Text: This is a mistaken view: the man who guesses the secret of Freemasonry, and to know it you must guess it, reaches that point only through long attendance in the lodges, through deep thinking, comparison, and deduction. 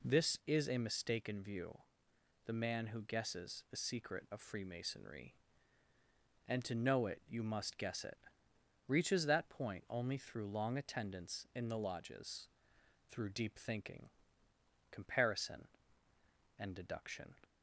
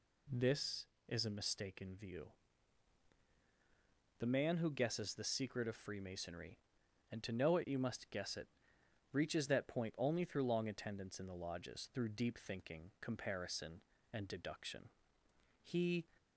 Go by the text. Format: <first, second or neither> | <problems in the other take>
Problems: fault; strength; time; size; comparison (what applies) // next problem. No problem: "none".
first | goes on to say "He"; slight; from 15.6 s on; 0.42 s long